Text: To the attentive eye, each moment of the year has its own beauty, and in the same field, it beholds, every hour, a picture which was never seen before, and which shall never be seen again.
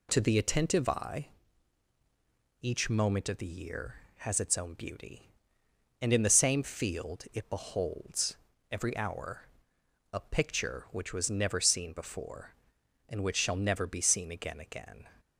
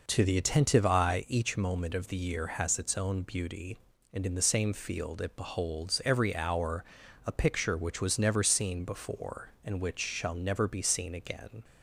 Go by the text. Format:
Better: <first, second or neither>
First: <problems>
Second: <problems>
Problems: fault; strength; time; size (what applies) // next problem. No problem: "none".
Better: second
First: says "again" twice; at 14.5 s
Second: none